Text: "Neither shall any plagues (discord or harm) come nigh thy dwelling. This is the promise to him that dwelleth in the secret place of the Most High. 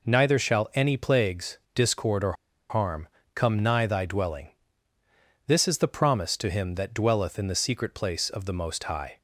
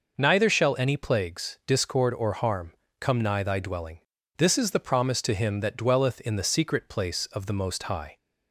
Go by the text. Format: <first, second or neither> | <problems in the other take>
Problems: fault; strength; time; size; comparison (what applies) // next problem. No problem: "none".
second | pauses between "or" and "harm"; at 2.3 s; 0.36 s long